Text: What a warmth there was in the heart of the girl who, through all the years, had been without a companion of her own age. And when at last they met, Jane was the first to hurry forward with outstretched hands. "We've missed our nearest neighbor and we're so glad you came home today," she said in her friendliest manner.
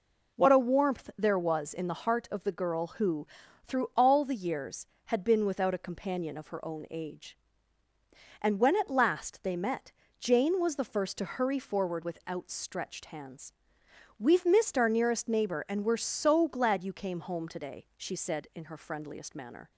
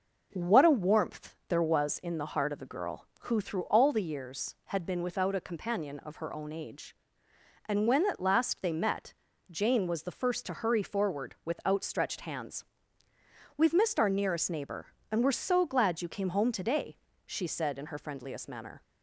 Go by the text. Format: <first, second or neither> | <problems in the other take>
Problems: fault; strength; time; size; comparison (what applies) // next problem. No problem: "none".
neither | none